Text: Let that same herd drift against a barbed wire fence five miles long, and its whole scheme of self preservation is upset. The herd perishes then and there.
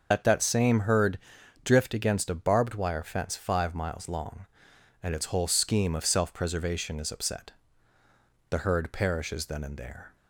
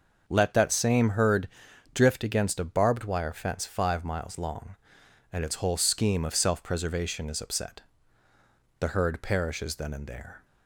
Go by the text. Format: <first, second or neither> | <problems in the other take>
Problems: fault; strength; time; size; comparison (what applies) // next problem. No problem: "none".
second | loses the start of "Let"; at 0.1 s; 115 ms // starts louder than the rest; until 1.1 s; 6.5 dB; also in the second // pauses between "herd" and "drift"; noticeable; at 1.1 s; 0.46 s long; noticeable in the second